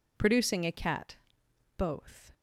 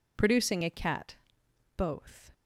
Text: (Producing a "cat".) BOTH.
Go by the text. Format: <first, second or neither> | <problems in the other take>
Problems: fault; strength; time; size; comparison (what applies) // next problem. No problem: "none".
neither | none